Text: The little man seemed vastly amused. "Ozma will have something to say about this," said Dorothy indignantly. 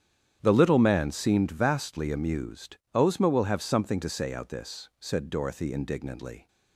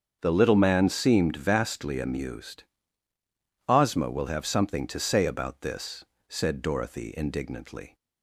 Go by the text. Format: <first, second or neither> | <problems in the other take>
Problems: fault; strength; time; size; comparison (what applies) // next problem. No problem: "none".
second | starts louder than the rest; strong; until 1.4 s; 9.5 dB; strong in the second // says "out" for "about"; at 4.3 s